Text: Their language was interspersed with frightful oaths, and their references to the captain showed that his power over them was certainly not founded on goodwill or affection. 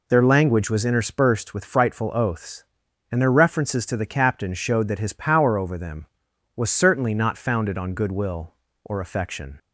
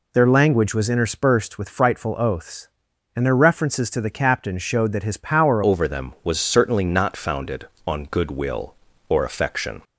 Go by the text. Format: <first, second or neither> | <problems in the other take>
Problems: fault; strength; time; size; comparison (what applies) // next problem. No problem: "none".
first | changes voice at "over"; from 5.6 s on; 4.2 s long